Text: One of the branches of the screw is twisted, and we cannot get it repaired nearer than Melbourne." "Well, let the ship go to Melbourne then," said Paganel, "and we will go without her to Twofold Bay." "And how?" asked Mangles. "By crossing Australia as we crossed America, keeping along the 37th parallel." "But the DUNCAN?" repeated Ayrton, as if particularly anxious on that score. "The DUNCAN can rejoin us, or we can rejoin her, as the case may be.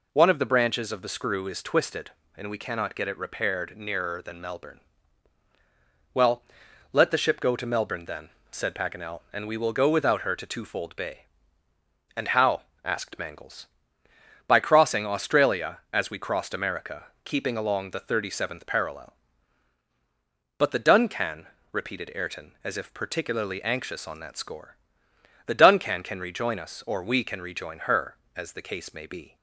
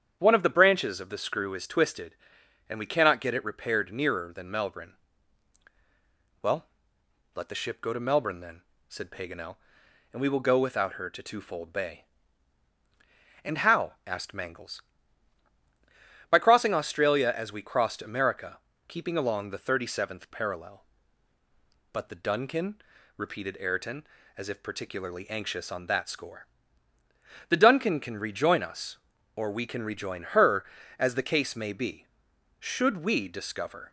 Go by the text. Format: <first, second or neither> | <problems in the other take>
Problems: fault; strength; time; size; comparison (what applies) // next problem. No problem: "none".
first | starts louder than the rest; strong; until 1.1 s; 8.5 dB // goes on to say "Should we discover"; noticeable; from 32.6 s on; 1.3 s long